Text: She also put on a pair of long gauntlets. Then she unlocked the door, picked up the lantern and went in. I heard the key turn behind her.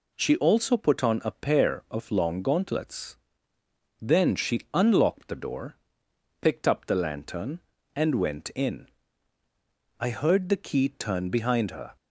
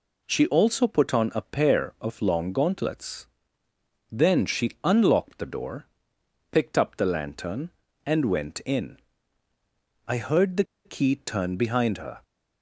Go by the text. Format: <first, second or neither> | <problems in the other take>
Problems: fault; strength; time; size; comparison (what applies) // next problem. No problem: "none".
first | pauses between "the" and "key"; slight; at 10.6 s; 0.21 s long